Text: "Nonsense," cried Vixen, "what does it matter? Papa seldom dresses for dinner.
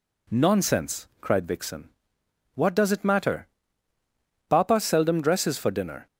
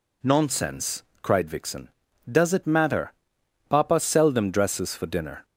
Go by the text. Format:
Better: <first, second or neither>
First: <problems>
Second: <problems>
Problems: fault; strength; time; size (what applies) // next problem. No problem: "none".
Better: first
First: none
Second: skips "what"; at 2.0 s